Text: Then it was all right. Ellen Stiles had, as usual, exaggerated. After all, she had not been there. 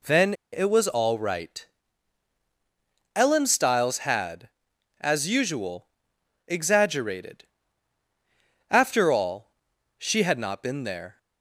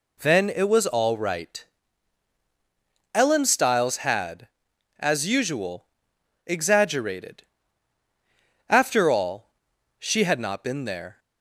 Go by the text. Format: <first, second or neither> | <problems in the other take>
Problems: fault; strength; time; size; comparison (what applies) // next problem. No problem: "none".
second | pauses between "Then" and "it"; slight; at 0.3 s; 0.19 s long